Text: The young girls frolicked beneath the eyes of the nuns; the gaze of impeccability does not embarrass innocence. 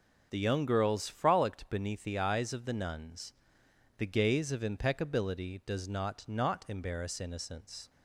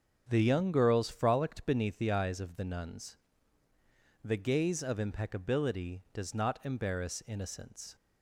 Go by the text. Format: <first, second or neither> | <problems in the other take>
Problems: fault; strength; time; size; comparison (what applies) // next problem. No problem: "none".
second | starts louder than the rest; until 1.3 s; 7 dB; strong in the second // says "not" twice; at 6.2 s